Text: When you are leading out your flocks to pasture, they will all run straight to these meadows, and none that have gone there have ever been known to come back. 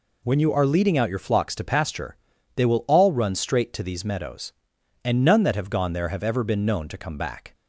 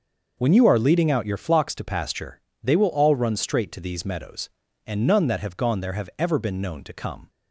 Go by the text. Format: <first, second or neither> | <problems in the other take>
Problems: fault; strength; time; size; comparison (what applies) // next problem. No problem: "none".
first | stops before "back"; at 7.2 s